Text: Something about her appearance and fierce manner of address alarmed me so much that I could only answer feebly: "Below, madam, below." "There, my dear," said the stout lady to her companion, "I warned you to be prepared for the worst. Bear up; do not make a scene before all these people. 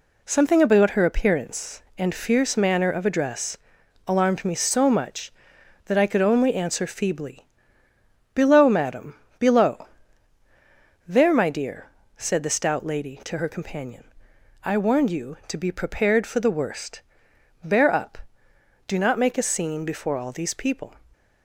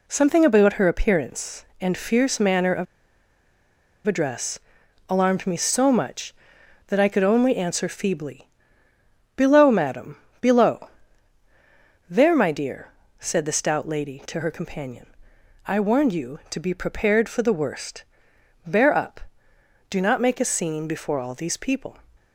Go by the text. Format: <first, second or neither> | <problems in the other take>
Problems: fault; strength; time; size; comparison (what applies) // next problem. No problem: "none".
first | pauses between "of" and "address"; at 2.8 s; 1.2 s long // pauses between "address" and "alarmed"; noticeable; at 4.5 s; 0.50 s long; noticeable in the first